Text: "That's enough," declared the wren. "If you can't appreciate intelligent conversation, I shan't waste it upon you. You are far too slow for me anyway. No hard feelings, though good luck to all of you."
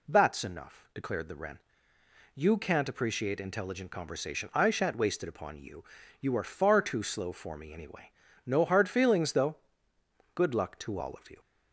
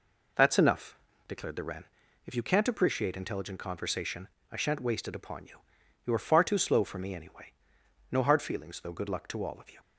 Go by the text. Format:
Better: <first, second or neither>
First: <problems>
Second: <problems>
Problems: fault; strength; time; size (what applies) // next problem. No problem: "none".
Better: second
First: skips "If"; at 1.9 s // pauses between "though" and "good"; noticeable; at 9.5 s; 0.78 s long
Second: none